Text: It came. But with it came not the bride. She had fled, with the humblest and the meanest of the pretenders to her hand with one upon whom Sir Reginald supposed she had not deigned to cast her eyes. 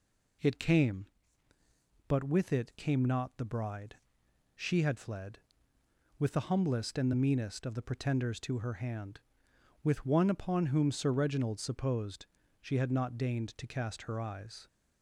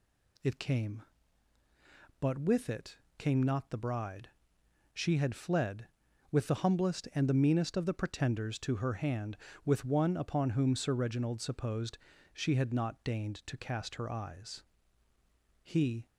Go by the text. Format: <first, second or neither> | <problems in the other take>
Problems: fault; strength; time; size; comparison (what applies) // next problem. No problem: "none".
first | pauses between "it" and "came"; slight; at 2.9 s; 0.22 s long // pauses between "supposed" and "she"; at 11.9 s; 0.36 s long; slight in the first // goes on to say "He"; slight; from 15.6 s on; 0.44 s long